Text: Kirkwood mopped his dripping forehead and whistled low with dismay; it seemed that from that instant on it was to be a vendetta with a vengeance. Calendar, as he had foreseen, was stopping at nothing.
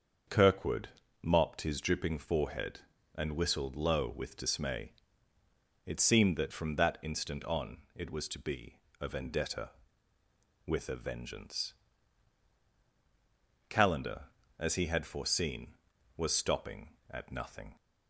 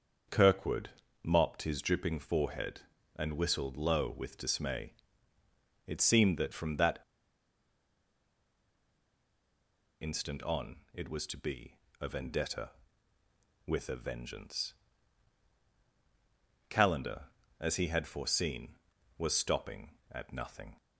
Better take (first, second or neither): first